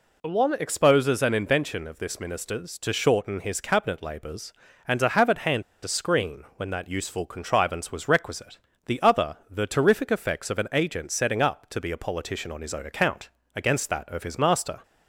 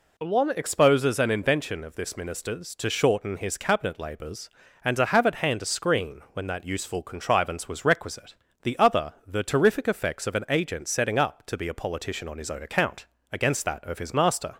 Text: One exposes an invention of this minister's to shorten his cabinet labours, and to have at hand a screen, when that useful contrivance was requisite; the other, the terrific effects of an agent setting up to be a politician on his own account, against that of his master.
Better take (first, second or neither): second